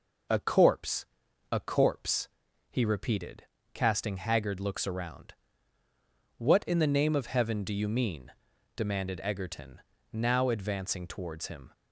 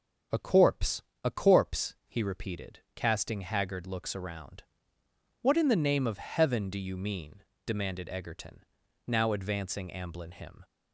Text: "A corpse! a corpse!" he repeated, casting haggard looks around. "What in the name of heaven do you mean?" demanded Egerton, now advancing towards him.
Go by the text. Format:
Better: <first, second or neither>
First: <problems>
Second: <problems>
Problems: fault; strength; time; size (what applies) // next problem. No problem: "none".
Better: first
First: none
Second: starts louder than the rest; until 1.5 s; 6.5 dB // says "amblin" for "towards"; at 9.8 s